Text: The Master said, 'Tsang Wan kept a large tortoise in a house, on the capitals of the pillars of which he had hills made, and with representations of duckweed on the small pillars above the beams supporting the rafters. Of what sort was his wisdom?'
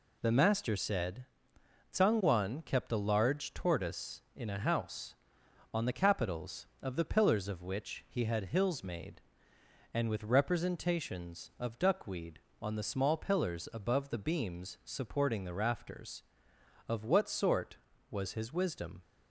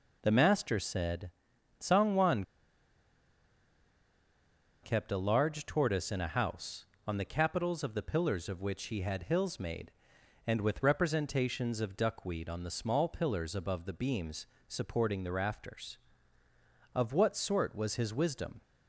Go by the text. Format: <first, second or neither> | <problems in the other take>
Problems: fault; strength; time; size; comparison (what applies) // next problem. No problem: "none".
first | pauses between "Wan" and "kept"; strong; at 2.4 s; 2.4 s long // pauses between "beams" and "supporting"; slight; at 14.4 s; 0.22 s long